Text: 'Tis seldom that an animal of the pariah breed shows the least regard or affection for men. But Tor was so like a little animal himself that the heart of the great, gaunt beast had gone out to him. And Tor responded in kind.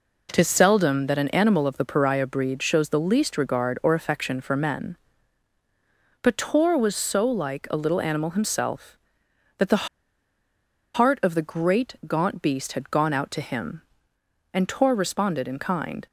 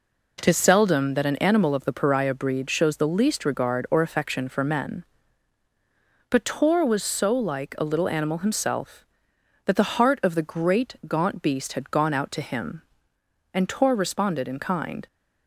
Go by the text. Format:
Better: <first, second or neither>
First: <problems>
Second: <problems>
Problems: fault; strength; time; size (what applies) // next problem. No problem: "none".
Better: second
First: pauses between "the" and "heart"; at 9.8 s; 1.0 s long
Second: none